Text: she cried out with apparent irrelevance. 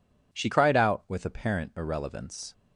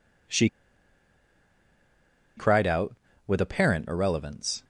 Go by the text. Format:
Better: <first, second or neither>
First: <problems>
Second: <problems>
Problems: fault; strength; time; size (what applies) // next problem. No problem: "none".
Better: first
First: none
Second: pauses between "she" and "cried"; strong; at 0.4 s; 1.9 s long